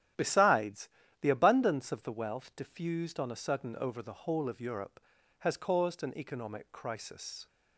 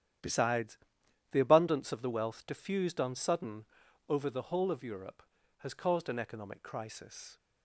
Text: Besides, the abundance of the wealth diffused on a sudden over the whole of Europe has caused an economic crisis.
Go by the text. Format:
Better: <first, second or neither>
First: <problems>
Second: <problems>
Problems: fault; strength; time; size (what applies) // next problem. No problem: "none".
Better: first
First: starts louder than the rest; strong; until 1.5 s; 11.5 dB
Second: starts louder than the rest; strong; until 1.7 s; 10.5 dB // skips "a"; at 3.1 s // pauses between "sudden" and "over"; at 3.6 s; 0.44 s long